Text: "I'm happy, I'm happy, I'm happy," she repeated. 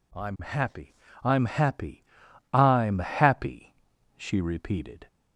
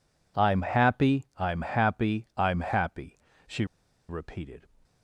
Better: first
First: none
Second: pauses between "she" and "repeated"; at 3.6 s; 0.43 s long

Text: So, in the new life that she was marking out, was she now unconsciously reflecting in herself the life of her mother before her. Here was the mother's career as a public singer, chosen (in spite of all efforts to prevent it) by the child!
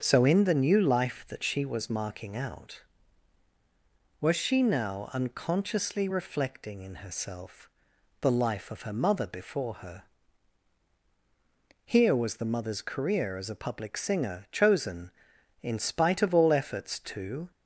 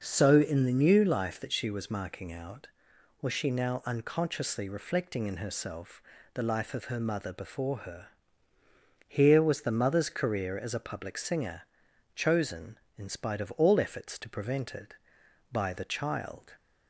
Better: second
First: starts louder than the rest; until 1.0 s; 7 dB // pauses between "herself" and "the"; noticeable; at 7.6 s; 0.52 s long // stops before "prevent it by the child"; at 17.5 s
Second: pauses between "herself" and "the"; slight; at 6.0 s; 0.32 s long

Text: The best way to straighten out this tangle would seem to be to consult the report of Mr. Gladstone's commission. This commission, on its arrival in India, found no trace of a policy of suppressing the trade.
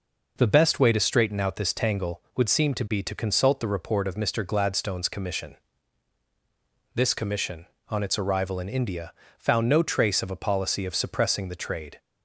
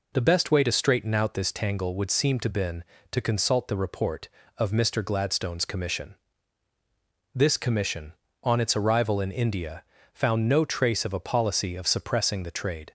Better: first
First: none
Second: says "been" for "be"; at 2.4 s

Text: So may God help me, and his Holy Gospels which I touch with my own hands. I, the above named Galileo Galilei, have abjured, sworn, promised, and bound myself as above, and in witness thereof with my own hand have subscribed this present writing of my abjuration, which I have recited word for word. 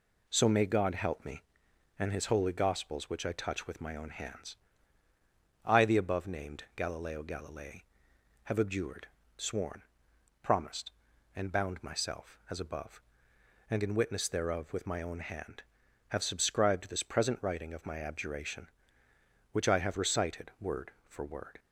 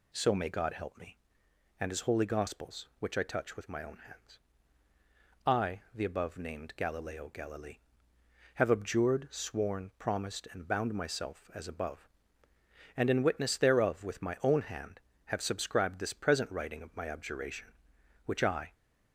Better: first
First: none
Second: stops before "have recited word for word"; at 18.7 s

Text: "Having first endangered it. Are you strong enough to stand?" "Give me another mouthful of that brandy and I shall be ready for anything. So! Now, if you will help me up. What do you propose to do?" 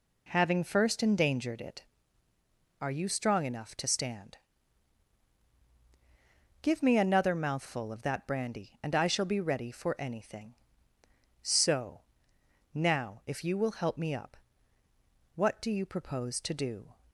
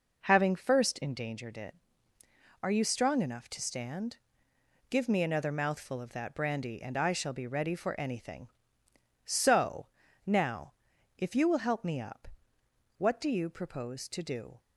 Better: neither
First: none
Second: none

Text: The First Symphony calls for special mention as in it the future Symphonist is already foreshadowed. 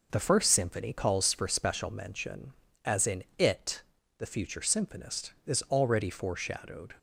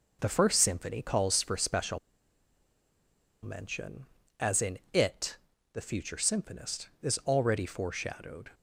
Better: first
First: pauses between "it" and "the"; slight; at 3.8 s; 0.34 s long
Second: pauses between "special" and "mention"; strong; at 1.9 s; 1.4 s long // pauses between "it" and "the"; slight; at 5.3 s; 0.34 s long

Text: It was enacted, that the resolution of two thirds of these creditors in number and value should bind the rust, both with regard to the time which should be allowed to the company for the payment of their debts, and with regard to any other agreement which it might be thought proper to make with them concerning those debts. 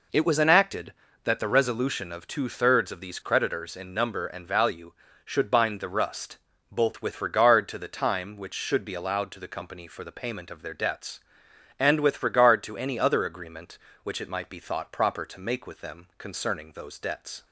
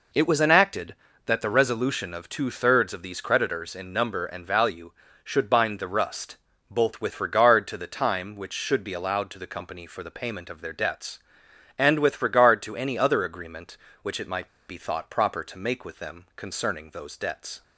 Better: first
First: none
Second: pauses between "might" and "be"; slight; at 14.4 s; 0.20 s long

